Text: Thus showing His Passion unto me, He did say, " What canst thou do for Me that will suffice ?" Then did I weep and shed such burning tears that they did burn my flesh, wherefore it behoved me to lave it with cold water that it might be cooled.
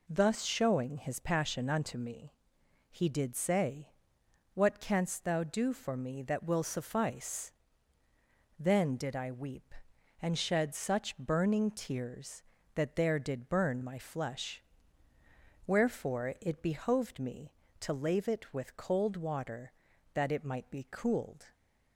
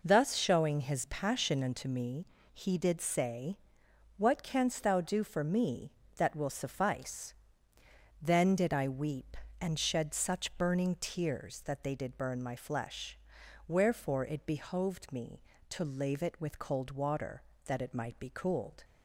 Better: second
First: says "there" for "they"; at 12.9 s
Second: none

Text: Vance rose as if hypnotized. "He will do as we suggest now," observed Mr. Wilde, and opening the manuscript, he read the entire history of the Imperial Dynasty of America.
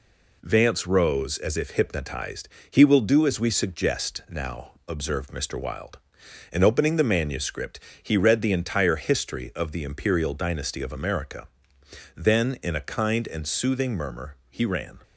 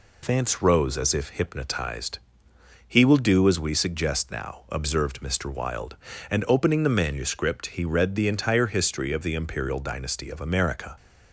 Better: second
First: goes on to say "Then in a kind and soothing murmur he ran"; strong; from 12.1 s on; 2.8 s long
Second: none

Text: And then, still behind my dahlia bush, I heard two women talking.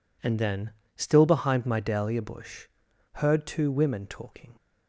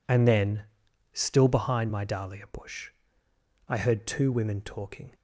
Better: second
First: skips "I"; at 2.8 s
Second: none

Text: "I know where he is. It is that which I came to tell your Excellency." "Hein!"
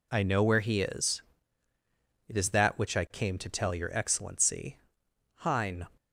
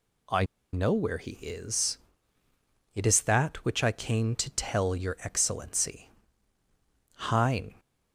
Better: first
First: none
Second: pauses between "I" and "know"; slight; at 0.4 s; 0.29 s long

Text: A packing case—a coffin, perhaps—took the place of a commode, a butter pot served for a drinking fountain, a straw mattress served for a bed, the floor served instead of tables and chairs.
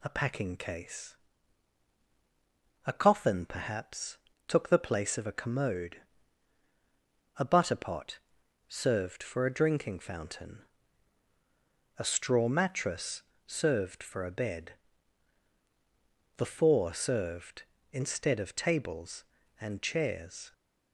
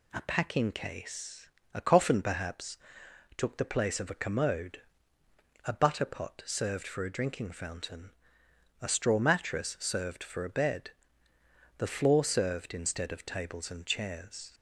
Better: second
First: pauses between "pot" and "served"; noticeable; at 8.1 s; 0.50 s long // pauses between "mattress" and "served"; slight; at 13.2 s; 0.24 s long // says "four" for "floor"; at 16.4 s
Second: none

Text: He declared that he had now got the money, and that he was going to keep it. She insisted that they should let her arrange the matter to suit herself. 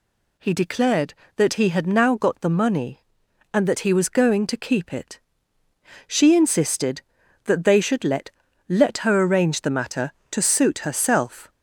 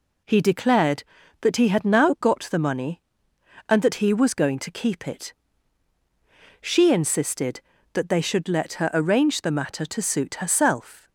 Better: second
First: says "let" twice; at 8.6 s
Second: none

